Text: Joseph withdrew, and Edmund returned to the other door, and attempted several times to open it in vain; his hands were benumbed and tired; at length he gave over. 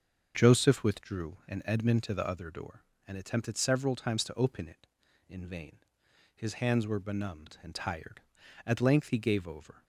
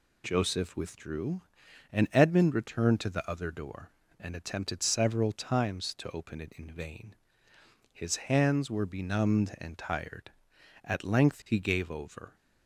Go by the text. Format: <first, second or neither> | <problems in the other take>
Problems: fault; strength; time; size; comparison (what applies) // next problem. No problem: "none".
second | starts louder than the rest; until 1.3 s; 6.5 dB // skips "returned"; at 2.0 s